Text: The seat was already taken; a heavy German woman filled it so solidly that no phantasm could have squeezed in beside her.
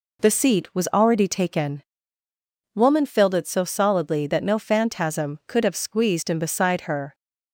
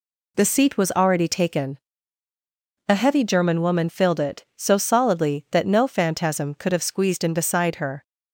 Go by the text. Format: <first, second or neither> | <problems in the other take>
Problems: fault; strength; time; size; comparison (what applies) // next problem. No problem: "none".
second | skips "a heavy German"; at 2.2 s